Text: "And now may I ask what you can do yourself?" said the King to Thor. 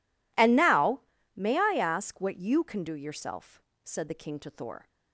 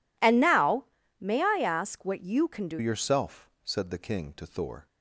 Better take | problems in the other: first | pauses between "now" and "may"; slight; at 0.8 s; 0.34 s long; slight in the first // changes voice at "yourself"; from 2.7 s on; 2.1 s long

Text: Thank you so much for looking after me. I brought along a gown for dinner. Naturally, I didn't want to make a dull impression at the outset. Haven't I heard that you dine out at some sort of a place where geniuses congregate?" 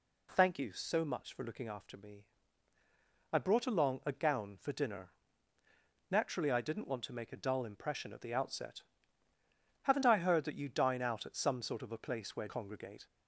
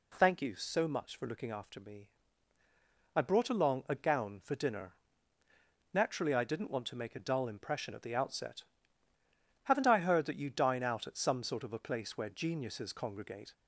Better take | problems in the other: second | skips "geniuses"; at 12.4 s

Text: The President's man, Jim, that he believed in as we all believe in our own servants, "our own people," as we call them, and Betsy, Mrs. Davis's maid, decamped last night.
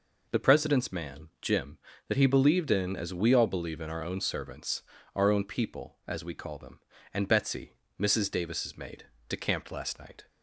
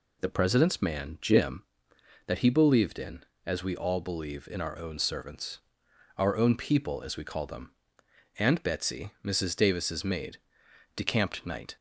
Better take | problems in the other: first | skips "last"; at 11.4 s

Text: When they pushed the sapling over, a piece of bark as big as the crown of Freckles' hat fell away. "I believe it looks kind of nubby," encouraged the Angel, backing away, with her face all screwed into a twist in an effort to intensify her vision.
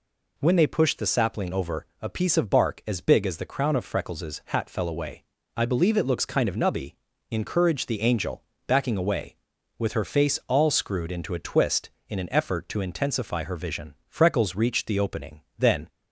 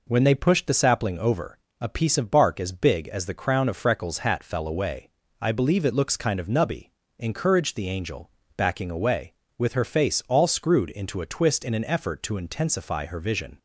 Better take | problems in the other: second | goes on to say "Freckles reached the opening then"; strong; from 14.0 s on; 1.8 s long

